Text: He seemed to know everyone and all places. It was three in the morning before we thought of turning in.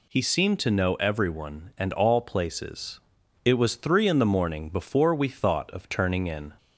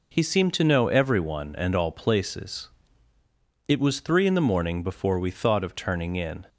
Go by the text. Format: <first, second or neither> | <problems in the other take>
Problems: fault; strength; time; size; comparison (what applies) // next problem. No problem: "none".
neither | none